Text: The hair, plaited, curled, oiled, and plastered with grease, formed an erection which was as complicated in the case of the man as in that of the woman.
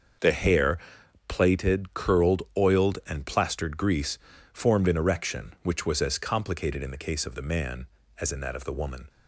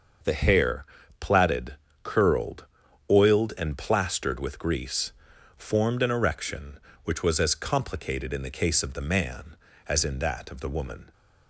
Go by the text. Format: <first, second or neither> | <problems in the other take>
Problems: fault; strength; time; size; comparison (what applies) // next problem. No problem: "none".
second | starts louder than the rest; until 1.6 s; 6.5 dB; also in the second // skips "with"; at 3.7 s